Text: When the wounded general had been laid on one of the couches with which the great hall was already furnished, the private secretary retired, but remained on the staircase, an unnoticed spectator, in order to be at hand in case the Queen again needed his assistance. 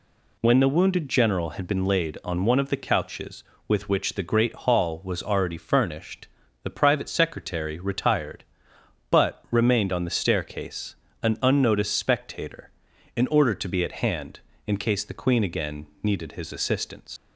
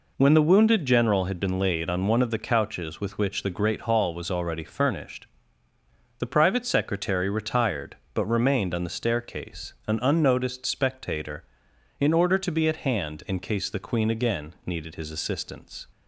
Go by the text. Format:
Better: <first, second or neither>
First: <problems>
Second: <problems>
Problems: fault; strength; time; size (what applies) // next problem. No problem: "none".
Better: second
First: pauses between "again" and "needed"; slight; at 15.8 s; 0.16 s long // leaves "assistance" unfinished; at 17.1 s; 80 ms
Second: none